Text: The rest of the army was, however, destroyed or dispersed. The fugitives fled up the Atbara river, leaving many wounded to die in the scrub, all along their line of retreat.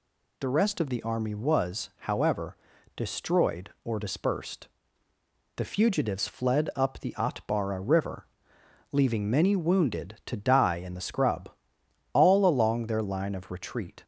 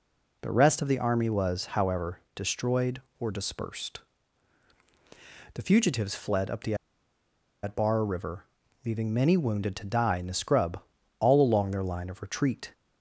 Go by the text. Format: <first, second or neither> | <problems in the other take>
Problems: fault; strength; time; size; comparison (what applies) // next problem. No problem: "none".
first | pauses between "the" and "Atbara"; noticeable; at 6.7 s; 0.88 s long